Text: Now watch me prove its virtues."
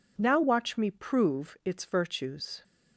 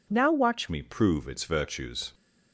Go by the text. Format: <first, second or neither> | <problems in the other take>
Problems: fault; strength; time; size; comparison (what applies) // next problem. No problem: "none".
first | changes voice at "me"; from 0.6 s on; 1.5 s long